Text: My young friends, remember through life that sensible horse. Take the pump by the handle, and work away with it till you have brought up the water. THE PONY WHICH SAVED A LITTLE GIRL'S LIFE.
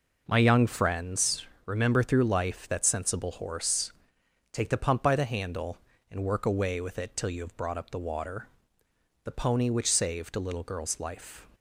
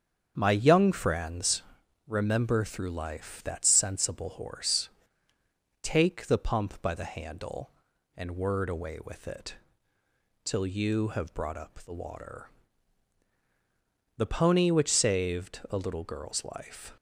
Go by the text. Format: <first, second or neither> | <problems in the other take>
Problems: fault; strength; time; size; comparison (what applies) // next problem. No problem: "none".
first | starts louder than the rest; strong; until 1.3 s; 7.5 dB // says "word" for "work"; at 8.3 s // pauses between "it" and "till"; noticeable; at 9.5 s; 0.88 s long